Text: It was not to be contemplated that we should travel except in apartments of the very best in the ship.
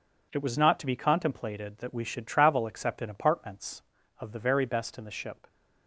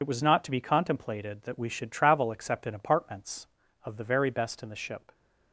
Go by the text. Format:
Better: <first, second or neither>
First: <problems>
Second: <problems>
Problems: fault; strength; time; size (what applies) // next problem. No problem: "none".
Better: first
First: none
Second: loses the start of "It"; at 0.0 s; 50 ms